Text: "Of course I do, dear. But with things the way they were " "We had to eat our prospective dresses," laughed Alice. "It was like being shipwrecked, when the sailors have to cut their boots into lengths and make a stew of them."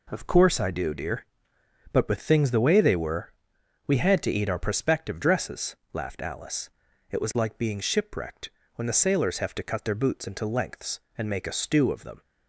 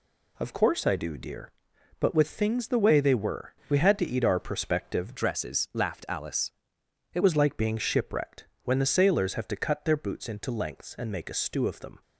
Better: first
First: none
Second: changes voice from "dresses" to "It"; from 5.1 to 7.2 s; 2.1 s long

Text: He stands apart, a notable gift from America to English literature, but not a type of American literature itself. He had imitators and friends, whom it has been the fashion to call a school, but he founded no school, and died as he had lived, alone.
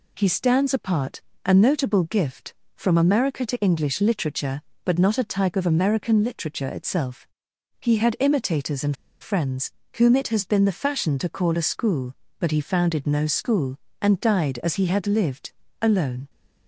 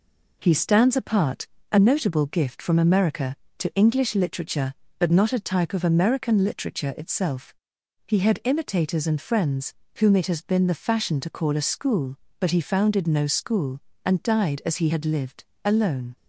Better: second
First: pauses between "and" and "friends"; slight; at 8.9 s; 0.26 s long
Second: none

